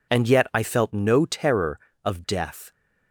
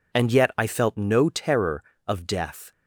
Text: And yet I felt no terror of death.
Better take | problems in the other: neither | none

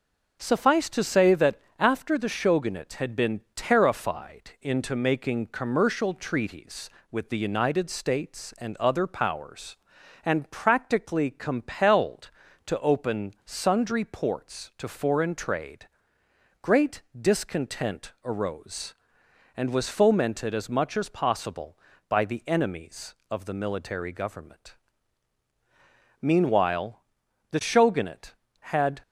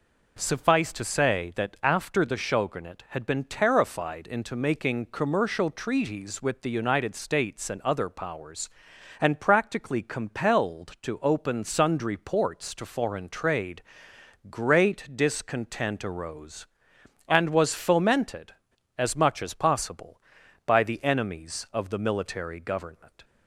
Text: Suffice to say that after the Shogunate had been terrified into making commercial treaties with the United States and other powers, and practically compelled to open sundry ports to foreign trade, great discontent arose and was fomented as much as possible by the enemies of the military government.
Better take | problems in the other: second | starts louder than the rest; until 1.4 s; 6.5 dB // pauses between "that" and "after"; slight; at 1.5 s; 0.24 s long // pauses between "great" and "discontent"; slight; at 17.0 s; 0.18 s long // goes on to say "Meanwhile the Shogunate had"; strong; from 26.2 s on; 2.7 s long

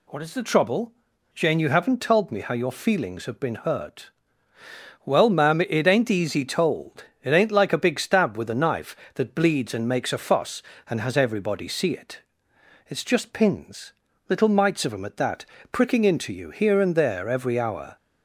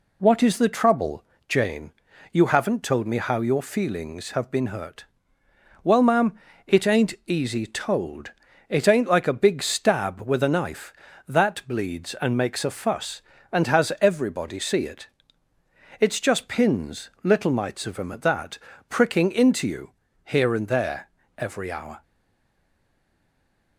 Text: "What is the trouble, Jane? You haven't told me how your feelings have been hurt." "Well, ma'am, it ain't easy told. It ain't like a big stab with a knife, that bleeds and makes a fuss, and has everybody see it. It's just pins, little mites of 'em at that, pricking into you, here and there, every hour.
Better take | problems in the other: first | stays silent after the last word; noticeable; from 22.0 s on; 1.7 s long

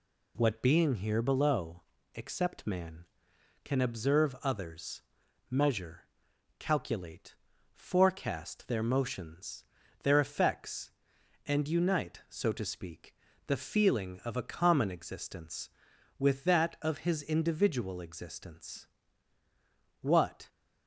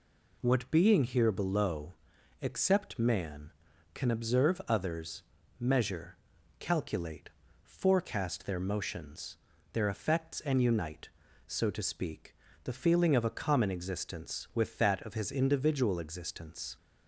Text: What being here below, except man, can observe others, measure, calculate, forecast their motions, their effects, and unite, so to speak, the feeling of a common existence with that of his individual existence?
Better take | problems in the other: second | goes on to say "What"; slight; from 20.0 s on; 0.48 s long

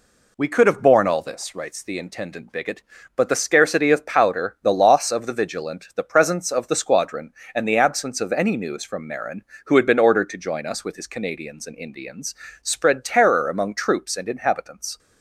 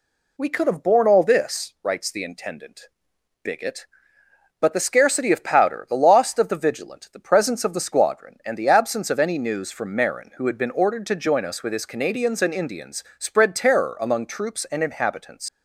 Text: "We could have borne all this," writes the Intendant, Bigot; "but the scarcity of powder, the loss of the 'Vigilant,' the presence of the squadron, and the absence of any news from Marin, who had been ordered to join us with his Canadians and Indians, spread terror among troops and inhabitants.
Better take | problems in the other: first | leaves "inhabitants" unfinished; at 15.4 s; 100 ms

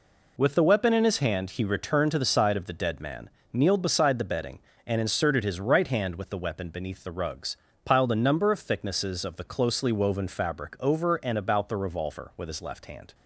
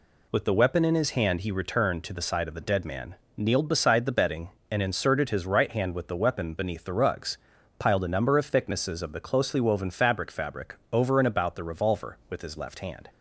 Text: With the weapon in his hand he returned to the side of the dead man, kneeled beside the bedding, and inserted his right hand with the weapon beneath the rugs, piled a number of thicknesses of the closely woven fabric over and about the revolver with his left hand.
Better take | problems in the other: first | says "fabric" twice; at 10.3 s

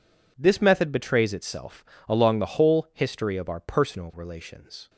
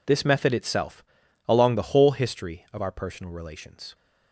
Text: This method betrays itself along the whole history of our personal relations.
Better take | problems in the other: first | skips "betrays"; at 0.5 s // pauses between "itself" and "along"; noticeable; at 1.0 s; 0.46 s long; slight in the first

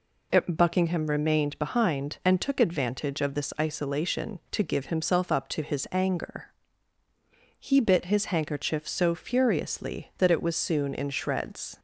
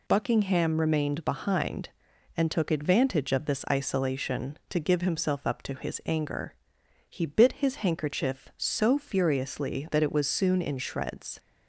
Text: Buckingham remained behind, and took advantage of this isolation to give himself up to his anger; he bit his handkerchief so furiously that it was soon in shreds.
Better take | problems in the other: neither | none

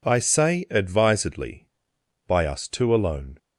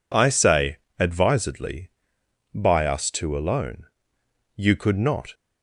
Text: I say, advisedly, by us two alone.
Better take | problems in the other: first | goes on to say "You could not"; noticeable; from 4.5 s on; 0.78 s long

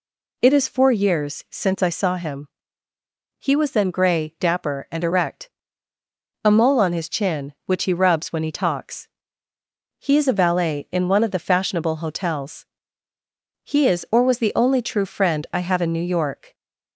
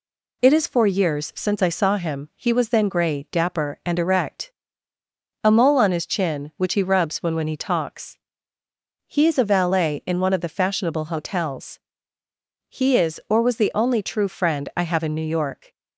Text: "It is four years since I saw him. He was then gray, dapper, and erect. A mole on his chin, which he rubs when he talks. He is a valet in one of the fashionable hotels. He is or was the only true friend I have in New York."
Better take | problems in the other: first | says "when" twice; at 7.3 s

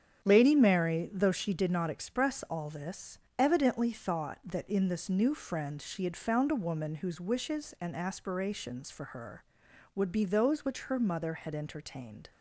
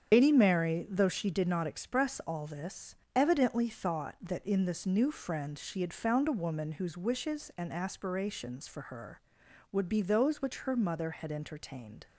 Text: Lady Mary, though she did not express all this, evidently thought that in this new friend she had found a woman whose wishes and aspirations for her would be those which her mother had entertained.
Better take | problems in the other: first | loses the start of "Lady"; at 0.1 s; 110 ms // starts louder than the rest; strong; until 1.1 s; 8 dB; strong in the first

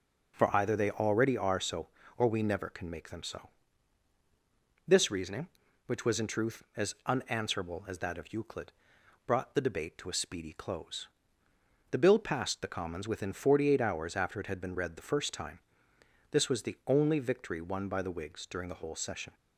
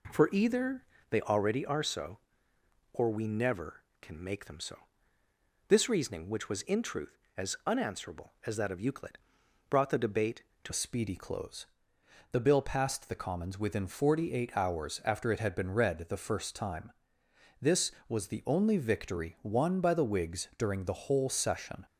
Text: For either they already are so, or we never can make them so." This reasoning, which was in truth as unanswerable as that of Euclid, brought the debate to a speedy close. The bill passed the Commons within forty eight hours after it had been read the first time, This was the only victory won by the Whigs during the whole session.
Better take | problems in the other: first | pauses between "either" and "they"; slight; at 0.8 s; 0.26 s long // changes voice at "a"; from 10.6 s on; 11.2 s long

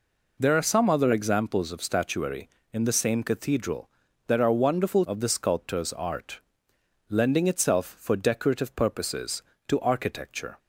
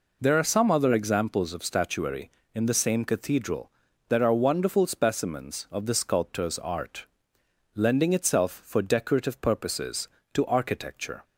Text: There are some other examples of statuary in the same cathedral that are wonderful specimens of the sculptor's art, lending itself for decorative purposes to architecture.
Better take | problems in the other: second | skips "specimens"; at 5.0 s

